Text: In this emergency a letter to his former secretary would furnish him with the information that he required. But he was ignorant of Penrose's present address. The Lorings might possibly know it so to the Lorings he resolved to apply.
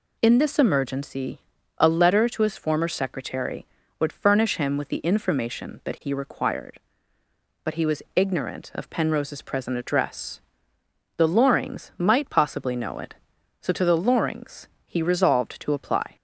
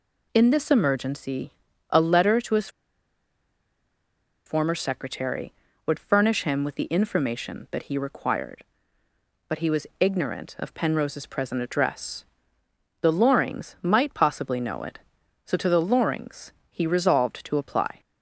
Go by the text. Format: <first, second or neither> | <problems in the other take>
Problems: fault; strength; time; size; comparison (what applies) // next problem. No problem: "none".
first | pauses between "emergency" and "a"; at 1.5 s; 0.38 s long; also in the first // pauses between "his" and "former"; strong; at 2.6 s; 1.7 s long // pauses between "Lorings" and "he"; slight; at 16.5 s; 0.18 s long; slight in the first